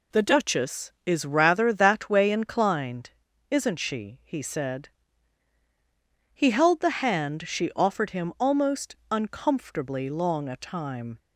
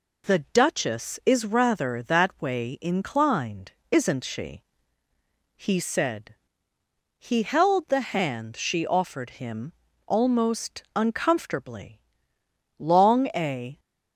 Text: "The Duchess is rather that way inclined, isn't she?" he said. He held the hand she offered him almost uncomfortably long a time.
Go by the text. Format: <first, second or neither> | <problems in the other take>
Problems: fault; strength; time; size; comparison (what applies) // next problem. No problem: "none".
first | pauses between "him" and "almost"; slight; at 9.7 s; 0.34 s long // pauses between "uncomfortably" and "long"; noticeable; at 11.9 s; 0.80 s long // stops before "time"; at 13.7 s